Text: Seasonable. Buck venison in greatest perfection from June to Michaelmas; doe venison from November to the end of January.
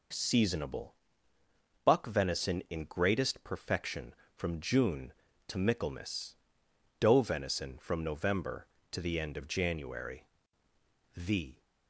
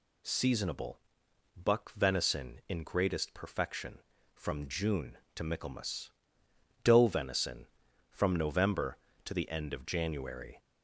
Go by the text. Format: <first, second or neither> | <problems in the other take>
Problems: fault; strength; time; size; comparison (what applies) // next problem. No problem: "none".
second | goes on to say "THE"; slight; from 11.1 s on; 0.46 s long